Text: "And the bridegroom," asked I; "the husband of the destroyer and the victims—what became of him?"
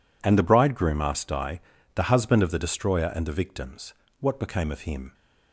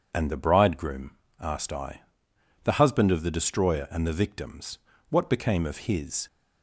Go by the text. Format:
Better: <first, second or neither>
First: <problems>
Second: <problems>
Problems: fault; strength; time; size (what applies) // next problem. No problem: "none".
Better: first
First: none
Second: says "his" for "him"; at 5.8 s